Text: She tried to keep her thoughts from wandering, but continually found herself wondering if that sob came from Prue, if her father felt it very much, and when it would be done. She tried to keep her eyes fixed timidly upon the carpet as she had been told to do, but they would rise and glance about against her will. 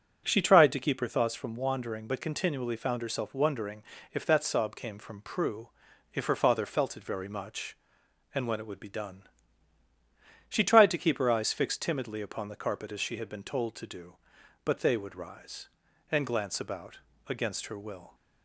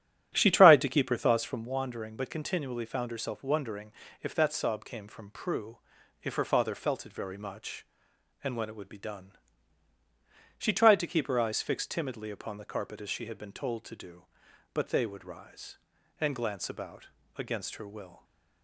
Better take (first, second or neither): first